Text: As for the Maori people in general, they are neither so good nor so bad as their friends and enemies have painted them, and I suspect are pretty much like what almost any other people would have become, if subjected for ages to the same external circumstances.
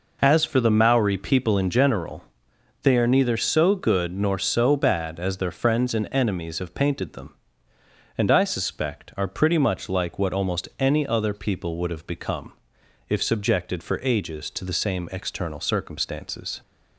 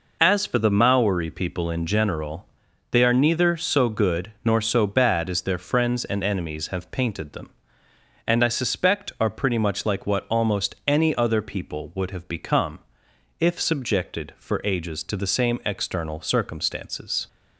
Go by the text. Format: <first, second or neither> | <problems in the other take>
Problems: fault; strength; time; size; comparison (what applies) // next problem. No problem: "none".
neither | none